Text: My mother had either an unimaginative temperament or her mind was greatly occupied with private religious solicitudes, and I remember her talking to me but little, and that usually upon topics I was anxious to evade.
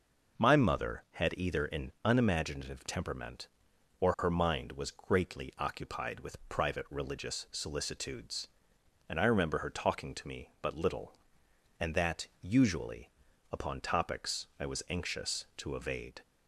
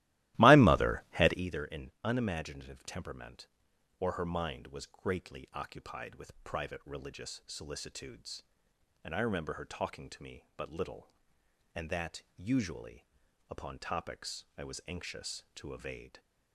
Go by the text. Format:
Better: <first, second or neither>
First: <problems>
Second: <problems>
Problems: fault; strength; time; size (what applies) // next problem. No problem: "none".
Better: first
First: pauses between "usually" and "upon"; at 13.0 s; 0.42 s long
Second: starts louder than the rest; strong; until 1.5 s; 16.5 dB // pauses between "usually" and "upon"; at 13.0 s; 0.44 s long